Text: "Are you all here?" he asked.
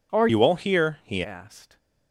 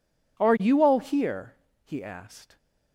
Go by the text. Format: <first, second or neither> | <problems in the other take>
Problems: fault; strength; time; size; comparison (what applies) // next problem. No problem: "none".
second | changes voice from "you" to "he"; from 0.2 to 1.2 s; 1.0 s long